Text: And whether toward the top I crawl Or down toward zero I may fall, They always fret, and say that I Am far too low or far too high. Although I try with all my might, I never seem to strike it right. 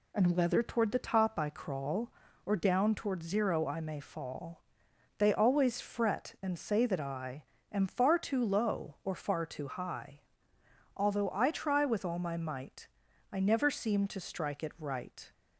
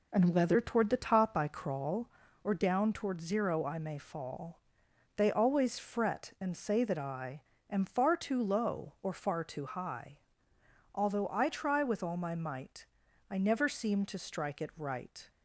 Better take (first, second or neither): first